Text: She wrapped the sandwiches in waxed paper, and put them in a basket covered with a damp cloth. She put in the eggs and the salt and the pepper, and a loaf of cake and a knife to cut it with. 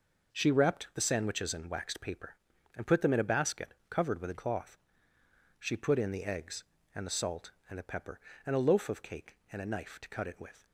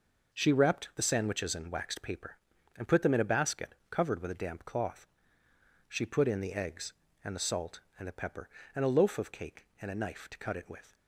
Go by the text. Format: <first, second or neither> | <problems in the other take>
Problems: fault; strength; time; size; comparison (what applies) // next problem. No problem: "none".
second | skips "damp"; at 4.3 s